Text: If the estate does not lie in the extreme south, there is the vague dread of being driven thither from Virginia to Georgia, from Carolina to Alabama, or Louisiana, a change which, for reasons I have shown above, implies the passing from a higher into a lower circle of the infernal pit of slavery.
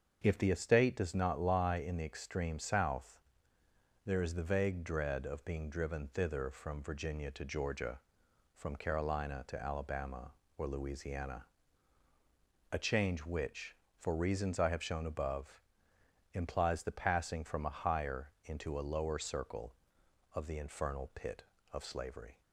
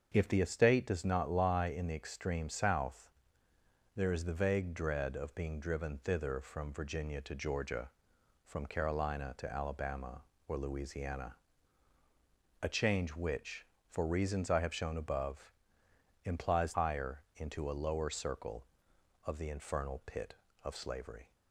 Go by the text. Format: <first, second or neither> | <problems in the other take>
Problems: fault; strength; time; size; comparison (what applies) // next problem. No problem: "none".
first | starts louder than the rest; until 1.1 s; 6.5 dB; also in the first // skips "the passing from a"; at 16.7 s